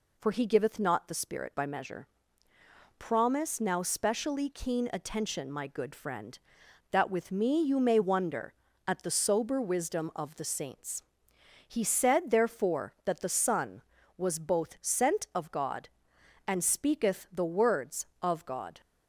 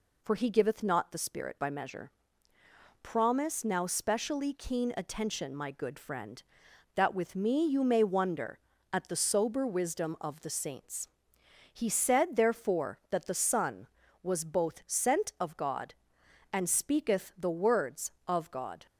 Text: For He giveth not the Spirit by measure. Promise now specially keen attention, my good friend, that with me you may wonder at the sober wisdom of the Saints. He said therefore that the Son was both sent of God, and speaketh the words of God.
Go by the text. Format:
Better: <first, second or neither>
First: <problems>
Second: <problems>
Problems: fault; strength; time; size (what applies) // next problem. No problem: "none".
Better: neither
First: none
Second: none